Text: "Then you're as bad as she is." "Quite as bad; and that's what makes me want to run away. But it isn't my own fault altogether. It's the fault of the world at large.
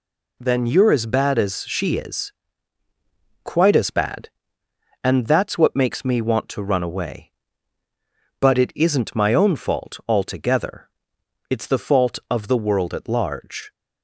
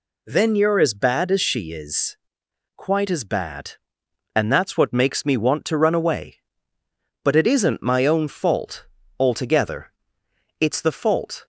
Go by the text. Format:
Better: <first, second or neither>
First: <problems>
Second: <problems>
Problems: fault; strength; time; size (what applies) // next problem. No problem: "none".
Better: first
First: none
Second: stops before "of the world at large"; at 11.4 s